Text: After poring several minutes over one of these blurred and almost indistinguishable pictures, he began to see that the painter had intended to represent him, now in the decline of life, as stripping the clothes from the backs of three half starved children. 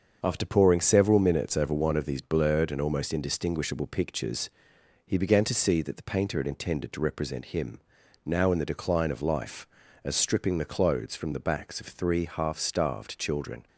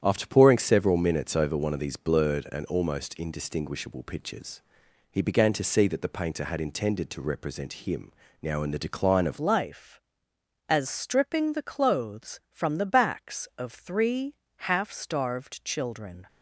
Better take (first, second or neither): first